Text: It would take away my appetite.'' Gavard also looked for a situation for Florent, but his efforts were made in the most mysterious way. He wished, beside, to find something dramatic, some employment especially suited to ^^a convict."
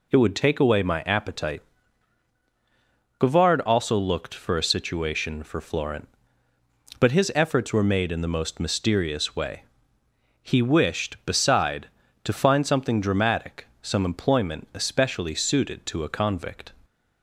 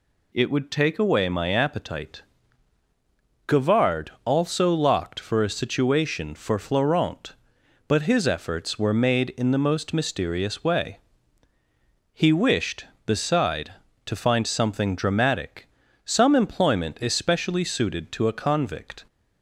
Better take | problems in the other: first | says "locked" for "looked"; at 4.7 s

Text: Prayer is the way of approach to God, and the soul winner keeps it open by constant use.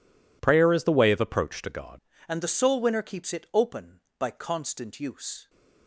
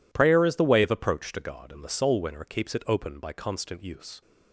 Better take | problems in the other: second | changes voice at "and"; from 2.2 s on; 3.2 s long

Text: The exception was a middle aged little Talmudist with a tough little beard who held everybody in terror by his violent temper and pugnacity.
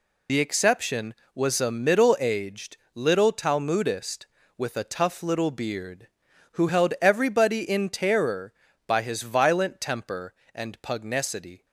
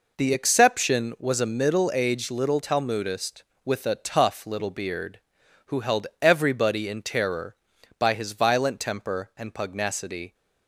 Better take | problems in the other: second | loses the start of "The"; at 0.2 s; 50 ms // pauses between "aged" and "little"; slight; at 2.7 s; 0.16 s long

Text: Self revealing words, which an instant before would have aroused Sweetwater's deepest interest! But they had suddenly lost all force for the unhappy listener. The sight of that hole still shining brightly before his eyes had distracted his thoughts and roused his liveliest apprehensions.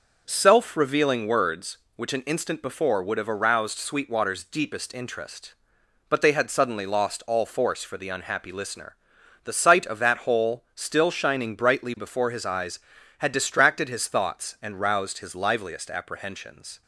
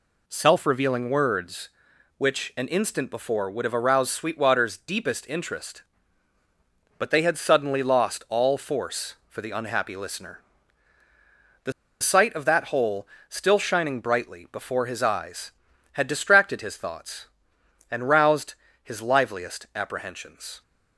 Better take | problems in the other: first | pauses between "The" and "sight"; slight; at 11.7 s; 0.29 s long // pauses between "hole" and "still"; slight; at 13.0 s; 0.20 s long // pauses between "roused" and "his"; slight; at 18.5 s; 0.30 s long

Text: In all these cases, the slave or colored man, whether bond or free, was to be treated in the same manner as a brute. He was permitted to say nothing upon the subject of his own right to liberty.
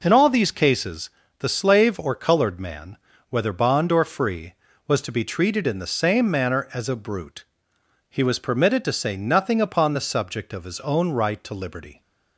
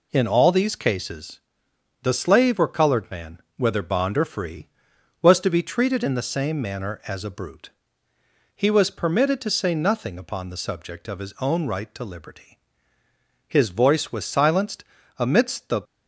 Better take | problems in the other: first | goes on to say "His voice was silenced amidst the"; strong; from 13.4 s on; 2.3 s long

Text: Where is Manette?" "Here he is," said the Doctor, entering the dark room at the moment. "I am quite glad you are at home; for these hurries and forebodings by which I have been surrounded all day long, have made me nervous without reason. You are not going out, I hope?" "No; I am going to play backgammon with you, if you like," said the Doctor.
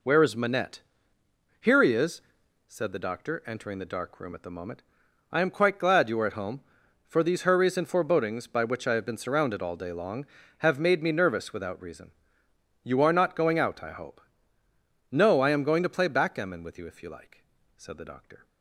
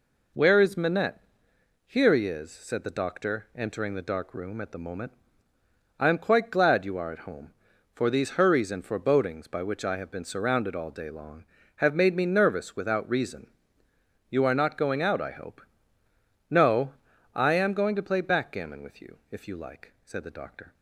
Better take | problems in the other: neither | none

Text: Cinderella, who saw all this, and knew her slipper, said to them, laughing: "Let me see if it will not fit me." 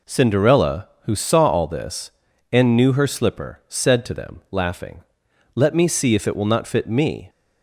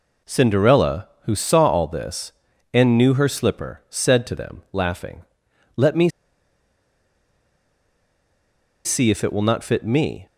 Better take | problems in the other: first | pauses between "me" and "see"; strong; at 6.0 s; 2.7 s long

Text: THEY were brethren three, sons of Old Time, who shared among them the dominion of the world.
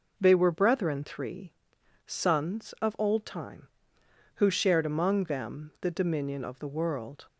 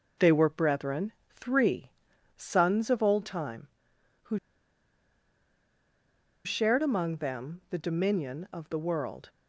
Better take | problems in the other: first | pauses between "brethren" and "three"; slight; at 1.1 s; 0.24 s long // pauses between "who" and "shared"; strong; at 4.3 s; 2.0 s long

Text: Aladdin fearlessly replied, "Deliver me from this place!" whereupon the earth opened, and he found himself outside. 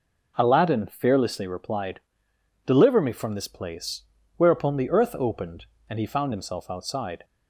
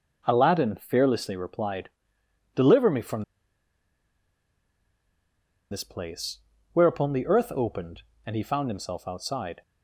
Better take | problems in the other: first | pauses between "from" and "this"; strong; at 3.2 s; 2.4 s long

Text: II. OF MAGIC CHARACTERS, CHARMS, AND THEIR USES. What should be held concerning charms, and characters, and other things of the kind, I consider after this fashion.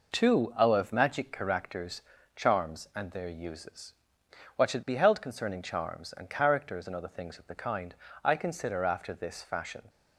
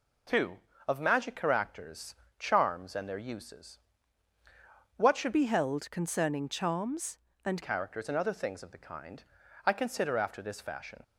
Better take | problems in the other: first | changes voice from "be" to "and"; from 5.3 to 7.6 s; 2.3 s long

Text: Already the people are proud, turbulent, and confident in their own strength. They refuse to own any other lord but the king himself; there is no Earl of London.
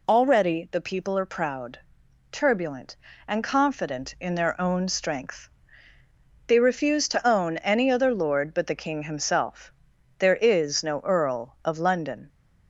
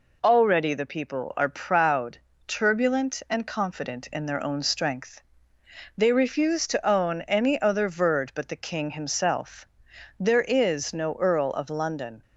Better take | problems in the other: first | says "verd" for "lord"; at 7.8 s

